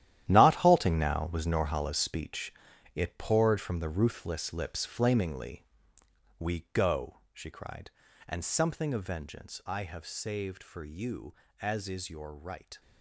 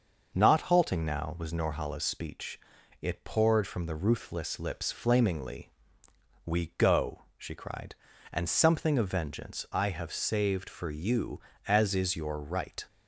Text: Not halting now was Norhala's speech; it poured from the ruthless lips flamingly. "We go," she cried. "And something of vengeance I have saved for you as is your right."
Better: second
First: gets quieter; strong; throughout; 12.5 dB // starts louder than the rest; strong; until 1.2 s; 12 dB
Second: starts louder than the rest; until 1.3 s; 6 dB

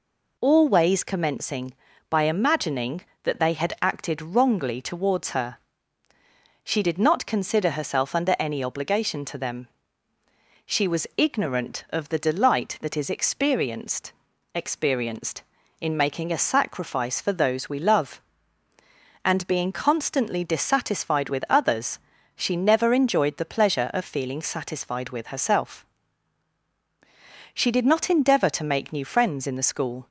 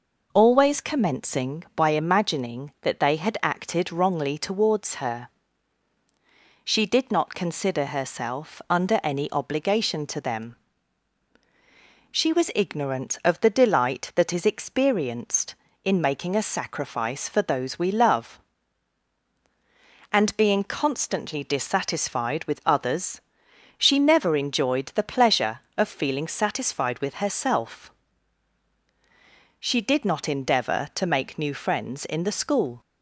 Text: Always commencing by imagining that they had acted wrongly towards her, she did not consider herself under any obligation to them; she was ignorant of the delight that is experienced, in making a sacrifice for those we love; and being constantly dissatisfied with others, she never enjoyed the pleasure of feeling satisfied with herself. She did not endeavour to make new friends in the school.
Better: second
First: says "experienced" twice; at 14.5 s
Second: none

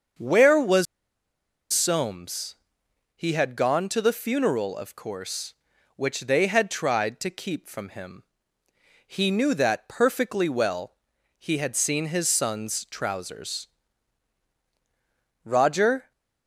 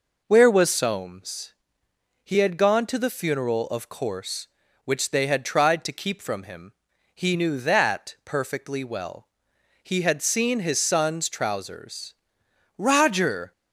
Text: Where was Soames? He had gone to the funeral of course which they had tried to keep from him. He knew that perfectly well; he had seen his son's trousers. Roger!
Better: second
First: starts louder than the rest; until 2.0 s; 7 dB // pauses between "was" and "Soames"; noticeable; at 0.8 s; 0.88 s long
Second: none

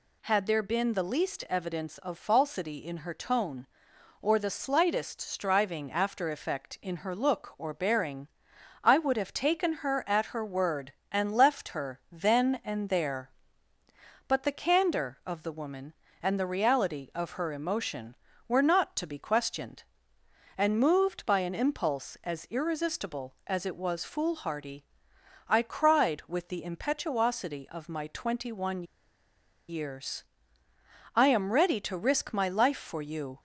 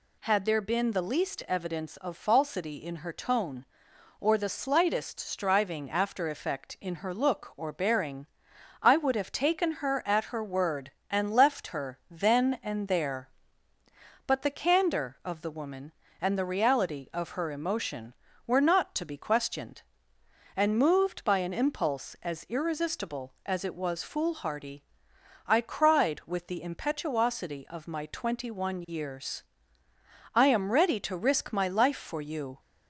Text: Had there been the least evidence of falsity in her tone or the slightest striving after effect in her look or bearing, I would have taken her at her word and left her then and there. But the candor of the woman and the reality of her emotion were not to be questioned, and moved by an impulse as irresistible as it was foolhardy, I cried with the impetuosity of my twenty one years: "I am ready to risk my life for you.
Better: second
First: pauses between "one" and "years"; noticeable; at 28.8 s; 0.85 s long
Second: none

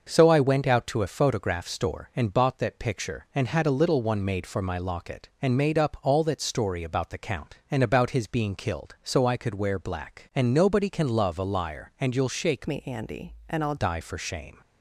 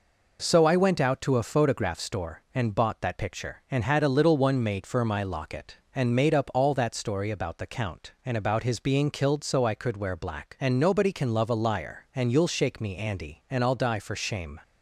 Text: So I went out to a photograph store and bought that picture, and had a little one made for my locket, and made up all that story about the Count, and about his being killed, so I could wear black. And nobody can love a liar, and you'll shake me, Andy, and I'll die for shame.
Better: second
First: starts louder than the rest; noticeable; until 1.1 s; 6 dB // changes voice from "me" to "I'll"; from 12.6 to 13.7 s; 1.1 s long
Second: none

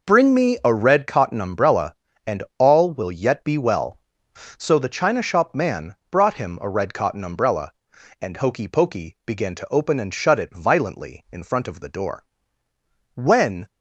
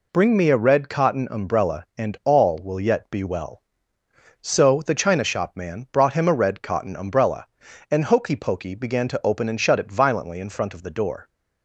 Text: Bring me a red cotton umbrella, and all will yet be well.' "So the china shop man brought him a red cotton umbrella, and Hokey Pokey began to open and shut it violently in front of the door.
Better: second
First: pauses between "man" and "brought"; slight; at 5.9 s; 0.16 s long // goes on to say "When"; from 13.1 s on; 0.54 s long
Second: none

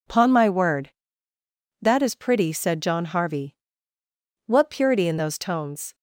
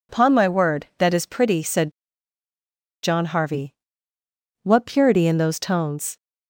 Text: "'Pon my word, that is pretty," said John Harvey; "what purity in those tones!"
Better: first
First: none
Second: pauses between "said" and "John"; at 1.9 s; 1.1 s long

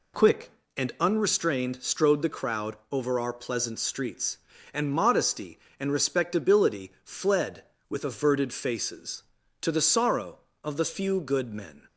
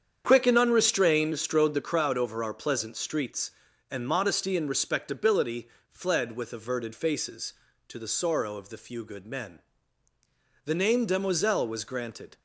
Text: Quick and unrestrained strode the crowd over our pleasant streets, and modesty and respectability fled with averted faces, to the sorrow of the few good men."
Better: first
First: none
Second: starts louder than the rest; strong; until 1.2 s; 8 dB // pauses between "respectability" and "fled"; slight; at 5.6 s; 0.20 s long // goes on to say "The name demoiselle was granted"; strong; from 10.6 s on; 1.7 s long

